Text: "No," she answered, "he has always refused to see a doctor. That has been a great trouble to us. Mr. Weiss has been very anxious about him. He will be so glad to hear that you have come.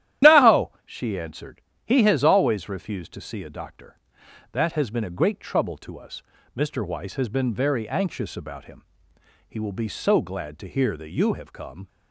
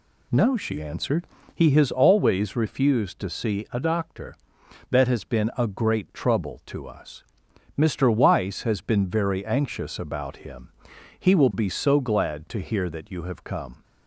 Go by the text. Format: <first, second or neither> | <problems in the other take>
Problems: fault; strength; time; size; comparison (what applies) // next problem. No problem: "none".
second | loses the start of "No"; at 0.2 s; 85 ms // starts louder than the rest; strong; until 1.3 s; 12 dB